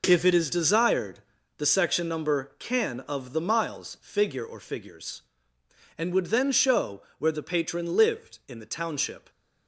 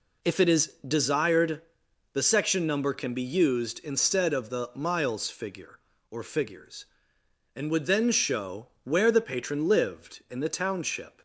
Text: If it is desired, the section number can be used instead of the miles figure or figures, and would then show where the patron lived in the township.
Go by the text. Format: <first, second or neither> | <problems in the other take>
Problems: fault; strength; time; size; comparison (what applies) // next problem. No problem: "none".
second | skips "be used instead"; at 2.9 s // pauses between "show" and "where"; slight; at 7.0 s; 0.16 s long; slight in the second